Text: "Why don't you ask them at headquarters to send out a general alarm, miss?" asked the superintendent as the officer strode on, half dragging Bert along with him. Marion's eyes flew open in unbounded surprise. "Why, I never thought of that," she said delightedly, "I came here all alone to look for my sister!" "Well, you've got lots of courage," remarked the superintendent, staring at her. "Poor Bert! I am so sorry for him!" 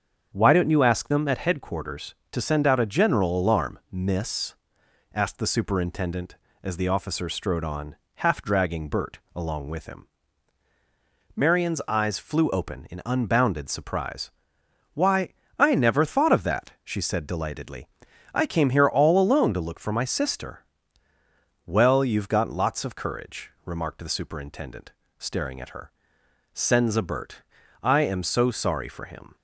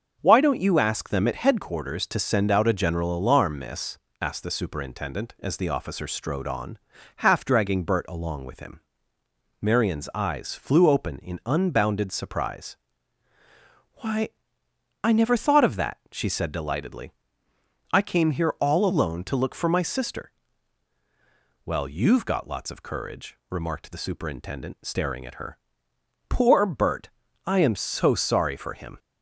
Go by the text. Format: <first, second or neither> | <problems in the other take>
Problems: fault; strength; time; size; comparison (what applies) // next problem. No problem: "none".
second | starts louder than the rest; strong; until 1.3 s; 7.5 dB; also in the second // pauses between "Bert" and "along"; slight; at 9.1 s; 0.16 s long // says "Senza" for "Poor"; at 26.5 s